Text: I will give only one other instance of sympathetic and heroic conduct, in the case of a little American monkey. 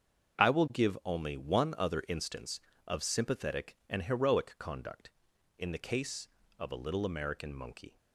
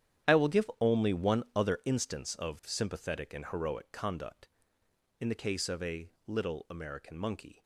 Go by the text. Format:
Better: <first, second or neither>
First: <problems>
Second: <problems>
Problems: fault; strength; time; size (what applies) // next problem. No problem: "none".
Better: first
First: starts louder than the rest; until 1.4 s; 7 dB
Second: gets quieter; strong; throughout; 15 dB // starts louder than the rest; strong; until 1.3 s; 10.5 dB // pauses between "a" and "little"; slight; at 6.1 s; 0.16 s long